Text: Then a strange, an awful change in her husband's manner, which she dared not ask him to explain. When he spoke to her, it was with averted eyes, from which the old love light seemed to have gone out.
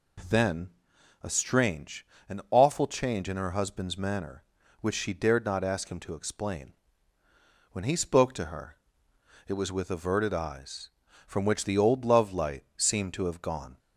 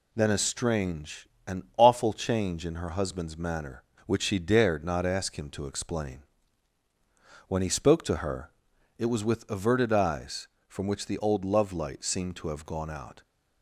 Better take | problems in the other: second | pauses between "Then" and "a"; noticeable; at 0.6 s; 0.54 s long // stops before "out"; at 13.7 s

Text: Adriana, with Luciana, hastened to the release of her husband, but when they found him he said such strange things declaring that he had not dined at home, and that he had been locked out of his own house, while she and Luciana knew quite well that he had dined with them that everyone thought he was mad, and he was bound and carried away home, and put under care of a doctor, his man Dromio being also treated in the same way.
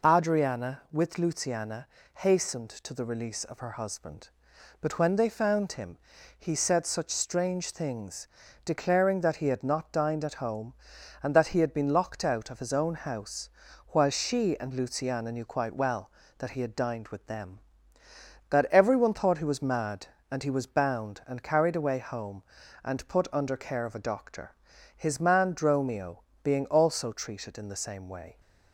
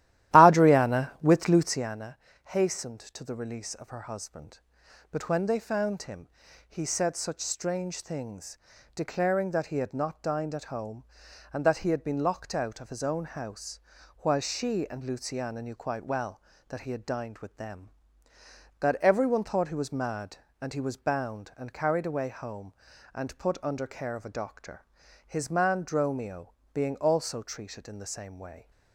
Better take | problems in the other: first | starts louder than the rest; strong; until 2.0 s; 14 dB // pauses between "him" and "he"; at 6.2 s; 0.40 s long; also in the first // pauses between "things" and "declaring"; at 8.5 s; 0.38 s long; also in the first // pauses between "Dromio" and "being"; slight; at 26.5 s; 0.18 s long; slight in the first

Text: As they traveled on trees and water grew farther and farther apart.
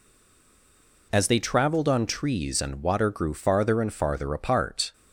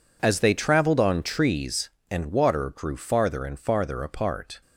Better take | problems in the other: second | stays silent before the first word; until 1.1 s; 1.1 s long

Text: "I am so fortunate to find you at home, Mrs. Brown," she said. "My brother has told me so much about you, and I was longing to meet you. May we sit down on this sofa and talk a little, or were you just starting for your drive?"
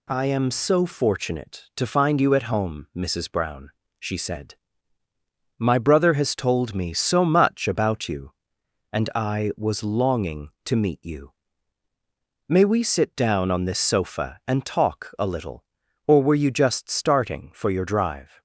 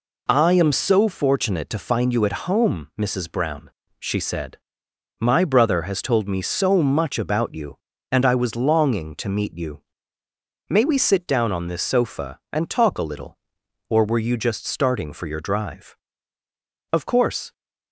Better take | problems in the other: first | goes on to say "Of course"; from 16.9 s on; 0.60 s long

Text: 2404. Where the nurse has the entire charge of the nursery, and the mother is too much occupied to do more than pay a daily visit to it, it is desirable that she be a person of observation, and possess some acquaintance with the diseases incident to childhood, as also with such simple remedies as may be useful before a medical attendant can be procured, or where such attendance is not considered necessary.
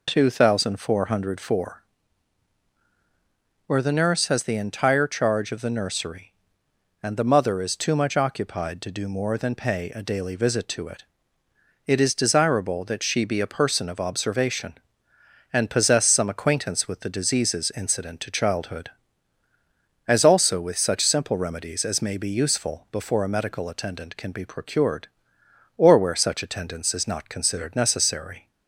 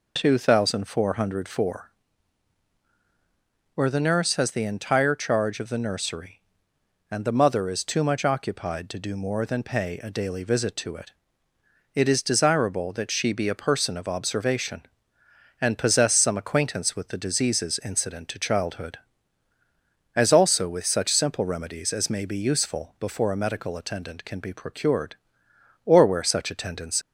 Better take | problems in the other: first | stops before "is not considered necessary"; at 27.0 s

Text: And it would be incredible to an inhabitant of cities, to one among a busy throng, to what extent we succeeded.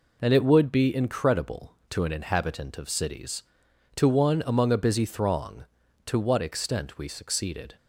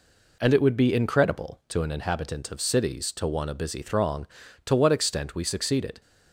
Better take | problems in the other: first | skips "among"; at 3.4 s

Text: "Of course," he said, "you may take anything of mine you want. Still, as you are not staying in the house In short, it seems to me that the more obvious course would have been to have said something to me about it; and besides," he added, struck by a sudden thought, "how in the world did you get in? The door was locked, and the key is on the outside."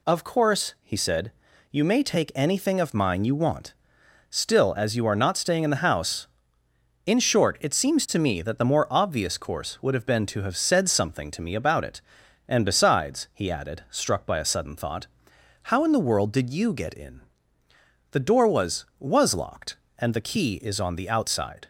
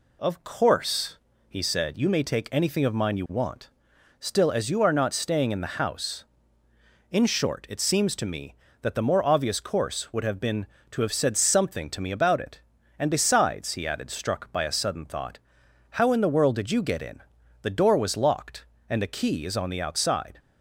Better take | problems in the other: second | says "was" twice; at 18.9 s

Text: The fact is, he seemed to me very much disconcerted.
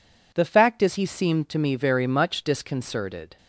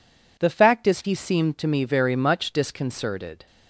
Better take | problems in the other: neither | none

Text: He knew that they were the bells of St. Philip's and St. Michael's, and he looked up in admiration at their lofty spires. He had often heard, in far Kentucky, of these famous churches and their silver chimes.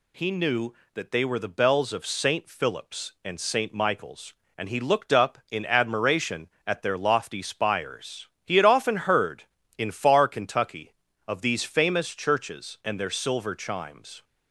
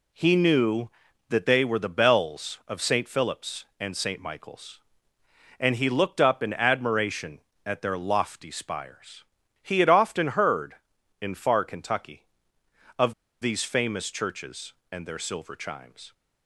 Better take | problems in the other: first | pauses between "of" and "these"; slight; at 13.1 s; 0.29 s long

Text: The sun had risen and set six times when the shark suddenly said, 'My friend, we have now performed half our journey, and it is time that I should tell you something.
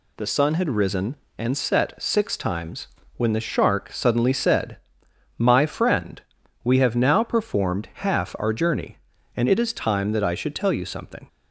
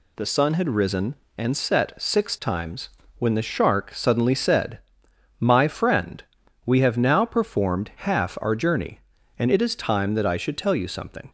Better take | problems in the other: neither | pauses between "times" and "when"; slight; the same in both

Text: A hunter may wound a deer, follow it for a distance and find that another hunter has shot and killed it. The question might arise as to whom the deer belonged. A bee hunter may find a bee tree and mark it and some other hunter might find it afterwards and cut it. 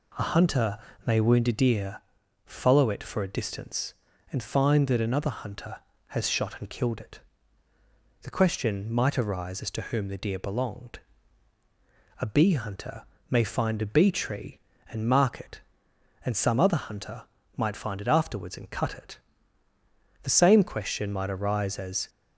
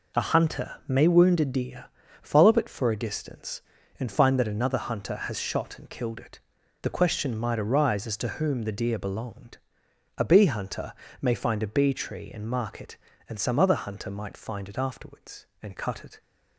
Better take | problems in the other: second | pauses between "hunter" and "may"; slight; at 0.7 s; 0.30 s long // pauses between "hunter" and "may"; slight; at 13.0 s; 0.26 s long; slight in the second // pauses between "hunter" and "might"; slight; at 17.2 s; 0.34 s long // goes on to say "The same question might arise as"; strong; from 20.2 s on; 1.8 s long

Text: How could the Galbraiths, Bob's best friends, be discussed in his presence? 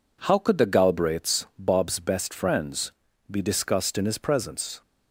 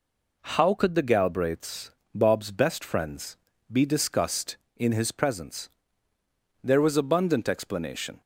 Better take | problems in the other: first | goes on to say "There was abundant explanation"; from 6.6 s on; 1.5 s long

